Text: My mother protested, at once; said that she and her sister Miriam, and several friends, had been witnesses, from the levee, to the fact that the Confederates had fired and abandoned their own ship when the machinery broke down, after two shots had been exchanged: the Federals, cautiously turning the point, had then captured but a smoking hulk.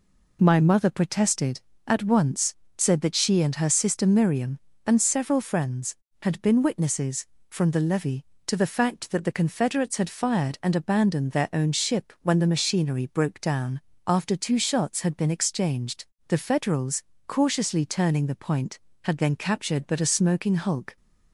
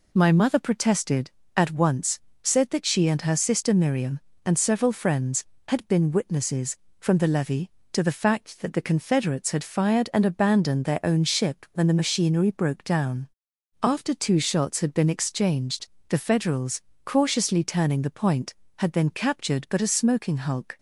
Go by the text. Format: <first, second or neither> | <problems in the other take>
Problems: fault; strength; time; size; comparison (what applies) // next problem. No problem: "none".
neither | none